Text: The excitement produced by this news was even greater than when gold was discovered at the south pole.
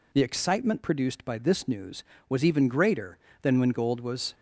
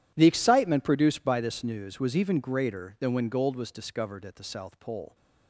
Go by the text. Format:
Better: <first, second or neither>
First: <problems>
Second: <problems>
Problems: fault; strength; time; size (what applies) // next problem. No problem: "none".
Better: second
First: stops before "discovered at the south pole"; at 4.3 s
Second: none